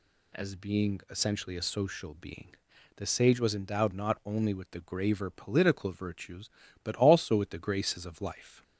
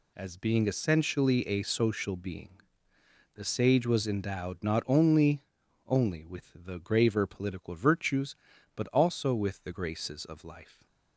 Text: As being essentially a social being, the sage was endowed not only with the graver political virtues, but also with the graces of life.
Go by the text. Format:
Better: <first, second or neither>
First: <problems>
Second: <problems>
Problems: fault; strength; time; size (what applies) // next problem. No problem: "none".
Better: first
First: none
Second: says "only" twice; at 5.8 s